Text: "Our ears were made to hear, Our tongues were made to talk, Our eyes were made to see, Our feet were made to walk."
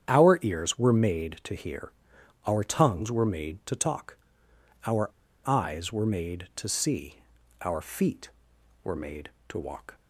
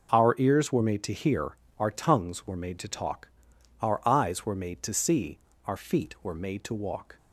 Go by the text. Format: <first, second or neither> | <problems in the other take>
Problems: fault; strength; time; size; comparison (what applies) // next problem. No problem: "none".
second | starts louder than the rest; strong; until 1.1 s; 8.5 dB // pauses between "Our" and "eyes"; at 5.0 s; 0.38 s long